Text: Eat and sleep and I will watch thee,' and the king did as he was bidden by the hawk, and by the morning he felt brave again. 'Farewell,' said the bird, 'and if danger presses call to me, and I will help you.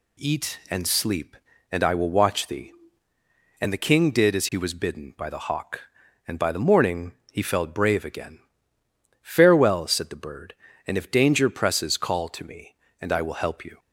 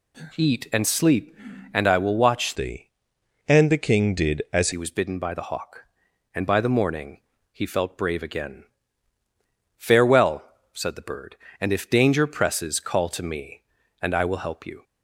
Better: first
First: pauses between "morning" and "he"; slight; at 7.1 s; 0.18 s long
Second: changes voice from "thee" to "as"; from 2.5 to 4.7 s; 2.2 s long // pauses between "morning" and "he"; slight; at 7.1 s; 0.32 s long

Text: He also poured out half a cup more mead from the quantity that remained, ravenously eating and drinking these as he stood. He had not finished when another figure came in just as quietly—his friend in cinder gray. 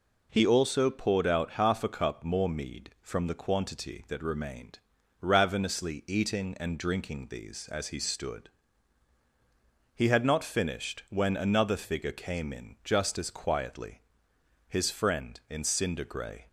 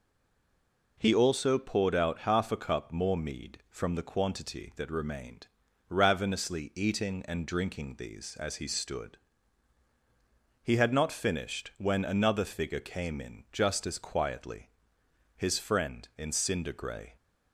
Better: first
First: none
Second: stays silent before the first word; slight; until 0.9 s; 0.9 s long

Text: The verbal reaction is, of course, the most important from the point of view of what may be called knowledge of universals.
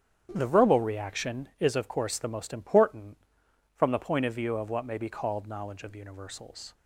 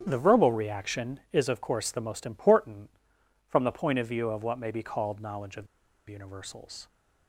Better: first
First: starts louder than the rest; strong; until 1.3 s; 9 dB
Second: starts louder than the rest; strong; until 1.0 s; 9 dB // pauses between "of" and "universals"; at 5.6 s; 0.43 s long

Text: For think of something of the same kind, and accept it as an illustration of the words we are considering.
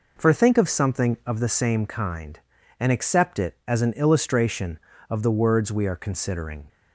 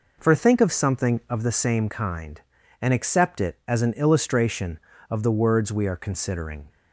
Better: neither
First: none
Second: none

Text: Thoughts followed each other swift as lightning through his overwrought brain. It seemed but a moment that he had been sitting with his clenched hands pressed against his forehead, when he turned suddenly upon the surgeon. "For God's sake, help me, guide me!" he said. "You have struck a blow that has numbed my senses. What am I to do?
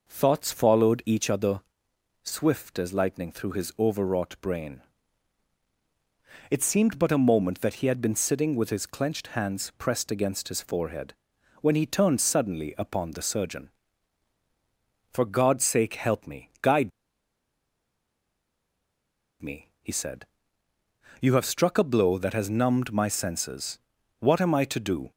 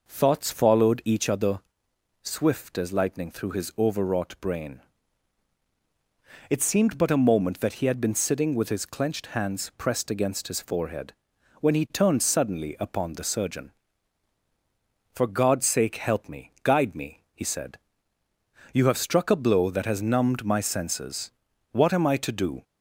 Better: second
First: pauses between "other" and "swift"; noticeable; at 1.6 s; 0.62 s long // pauses between "guide" and "me"; strong; at 16.9 s; 2.5 s long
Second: pauses between "other" and "swift"; noticeable; at 1.6 s; 0.62 s long

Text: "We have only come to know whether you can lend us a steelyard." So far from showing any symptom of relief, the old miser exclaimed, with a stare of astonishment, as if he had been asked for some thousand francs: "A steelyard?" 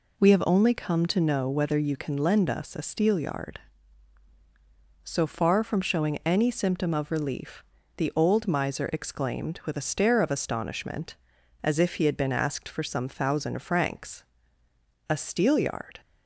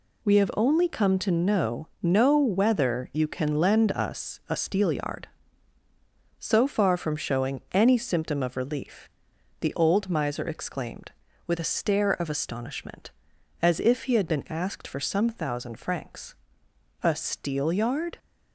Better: first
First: none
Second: says "know" twice; at 1.9 s

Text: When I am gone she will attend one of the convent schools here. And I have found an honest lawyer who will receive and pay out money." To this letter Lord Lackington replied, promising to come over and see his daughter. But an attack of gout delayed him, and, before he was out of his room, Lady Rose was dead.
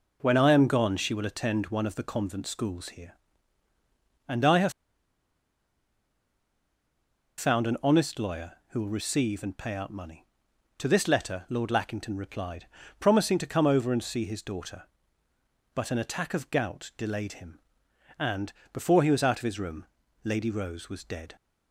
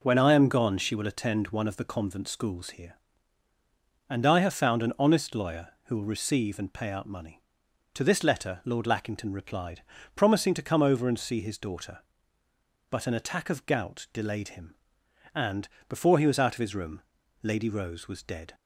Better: second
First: pauses between "have" and "found"; strong; at 4.7 s; 2.6 s long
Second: none

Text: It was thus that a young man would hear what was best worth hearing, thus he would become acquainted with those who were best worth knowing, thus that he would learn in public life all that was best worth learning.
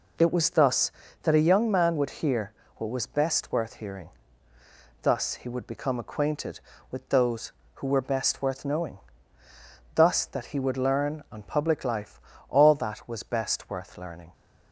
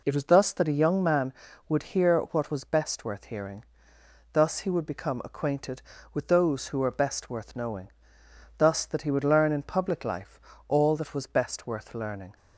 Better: second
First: pauses between "hear" and "what"; slight; at 2.5 s; 0.24 s long // says "on" for "in"; at 11.3 s // pauses between "life" and "all"; slight; at 12.2 s; 0.28 s long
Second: pauses between "life" and "all"; slight; at 10.3 s; 0.30 s long

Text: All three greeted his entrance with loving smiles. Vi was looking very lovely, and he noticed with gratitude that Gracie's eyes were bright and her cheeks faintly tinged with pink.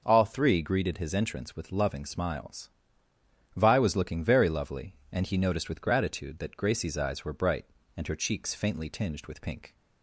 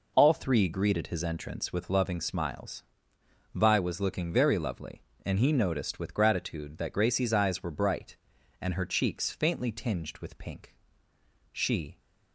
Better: first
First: none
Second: goes on to say "She"; slight; from 11.5 s on; 0.48 s long

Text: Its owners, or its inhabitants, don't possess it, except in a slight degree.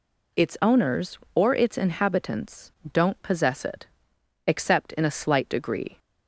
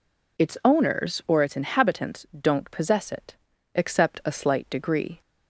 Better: first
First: none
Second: skips "in"; at 4.2 s

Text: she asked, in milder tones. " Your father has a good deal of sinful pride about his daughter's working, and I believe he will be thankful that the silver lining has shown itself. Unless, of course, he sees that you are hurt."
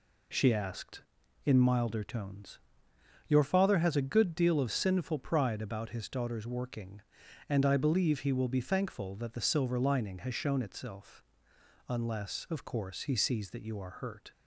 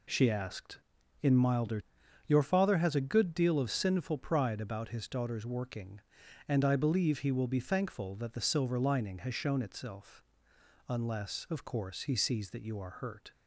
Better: first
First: none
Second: skips "tones"; at 1.8 s

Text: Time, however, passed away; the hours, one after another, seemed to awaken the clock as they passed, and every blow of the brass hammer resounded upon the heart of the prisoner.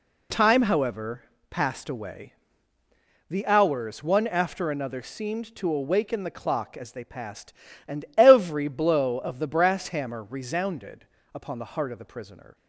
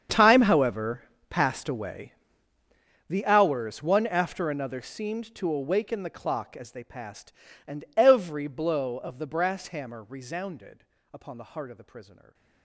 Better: first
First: pauses between "resounded" and "upon"; slight; at 11.0 s; 0.30 s long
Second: gets quieter; strong; throughout; 19 dB // pauses between "resounded" and "upon"; slight; at 10.8 s; 0.30 s long // stays silent after the last word; slight; from 12.1 s on; 0.5 s long

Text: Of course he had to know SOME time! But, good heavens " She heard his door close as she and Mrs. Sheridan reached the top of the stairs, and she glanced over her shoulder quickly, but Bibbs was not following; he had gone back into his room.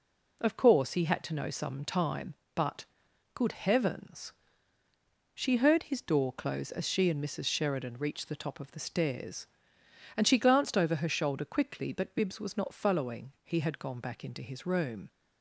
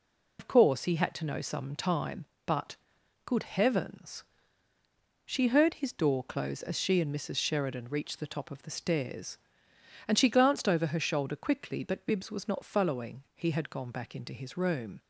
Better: first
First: none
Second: loses the start of "Of"; at 0.3 s; 85 ms

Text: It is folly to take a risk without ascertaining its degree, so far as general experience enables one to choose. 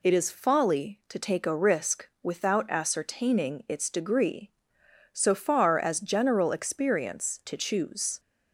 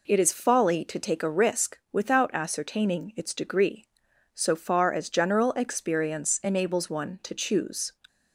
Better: second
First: pauses between "risk" and "without"; slight; at 2.0 s; 0.16 s long // skips "enables one"; at 7.4 s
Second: none

